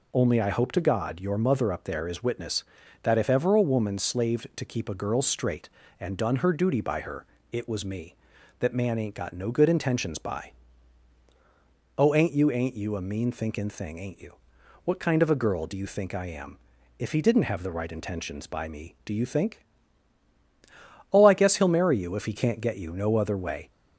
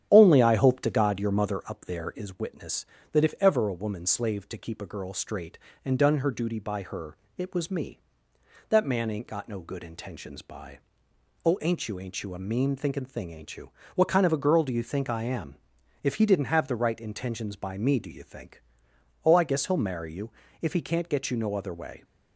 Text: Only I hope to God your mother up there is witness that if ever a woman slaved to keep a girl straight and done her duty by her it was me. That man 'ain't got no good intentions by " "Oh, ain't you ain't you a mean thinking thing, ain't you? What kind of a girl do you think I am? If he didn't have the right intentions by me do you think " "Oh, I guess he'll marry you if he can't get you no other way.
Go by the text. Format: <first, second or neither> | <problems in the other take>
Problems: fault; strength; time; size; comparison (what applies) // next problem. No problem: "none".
first | starts louder than the rest; strong; until 1.6 s; 10.5 dB // pauses between "her" and "it"; slight; at 7.1 s; 0.20 s long; slight in the first // pauses between "you" and "if"; slight; at 20.2 s; 0.32 s long